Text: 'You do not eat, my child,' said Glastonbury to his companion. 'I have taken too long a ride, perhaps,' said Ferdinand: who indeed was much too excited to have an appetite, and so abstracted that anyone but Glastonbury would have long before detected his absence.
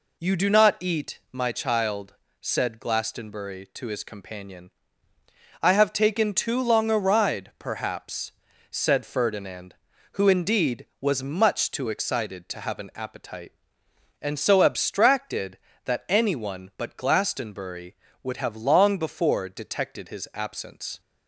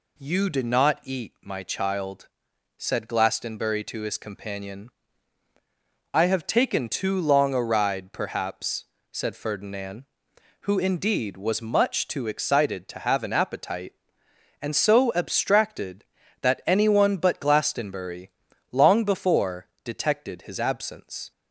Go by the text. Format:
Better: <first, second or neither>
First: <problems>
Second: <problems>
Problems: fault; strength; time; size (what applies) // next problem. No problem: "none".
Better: first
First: none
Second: skips "would have"; at 18.5 s // pauses between "before" and "detected"; slight; at 19.6 s; 0.16 s long